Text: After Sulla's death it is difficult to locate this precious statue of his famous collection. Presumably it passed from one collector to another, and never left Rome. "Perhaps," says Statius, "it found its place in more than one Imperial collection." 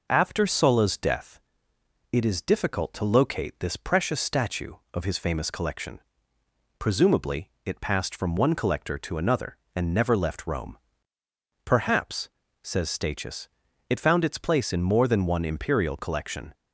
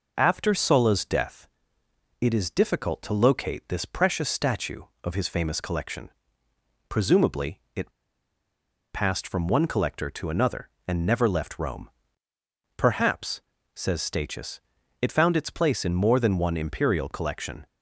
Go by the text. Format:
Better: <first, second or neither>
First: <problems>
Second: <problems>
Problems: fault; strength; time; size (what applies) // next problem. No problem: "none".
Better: first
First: pauses between "death" and "it"; noticeable; at 1.3 s; 0.73 s long // pauses between "Presumably" and "it"; slight; at 7.4 s; 0.16 s long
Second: pauses between "death" and "it"; noticeable; at 1.4 s; 0.74 s long // pauses between "Presumably" and "it"; slight; at 7.5 s; 0.16 s long // pauses between "it" and "passed"; at 7.8 s; 1.0 s long